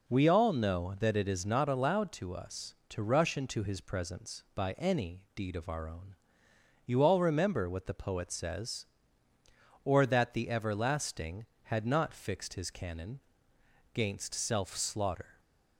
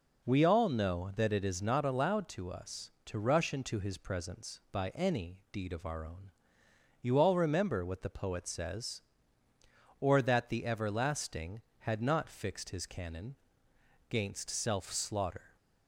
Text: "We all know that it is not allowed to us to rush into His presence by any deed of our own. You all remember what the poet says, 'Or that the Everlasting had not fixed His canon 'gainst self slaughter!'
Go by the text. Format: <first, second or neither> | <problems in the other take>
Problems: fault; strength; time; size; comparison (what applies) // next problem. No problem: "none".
neither | pauses between "canon" and "gainst"; noticeable; the same in both